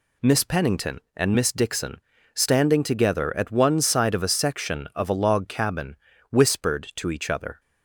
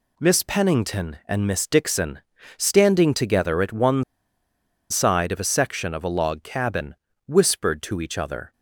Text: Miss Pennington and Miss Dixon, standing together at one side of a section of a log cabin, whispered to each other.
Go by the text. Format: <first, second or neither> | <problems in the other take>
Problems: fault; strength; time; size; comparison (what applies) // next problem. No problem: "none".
first | pauses between "one" and "side"; noticeable; at 4.0 s; 0.90 s long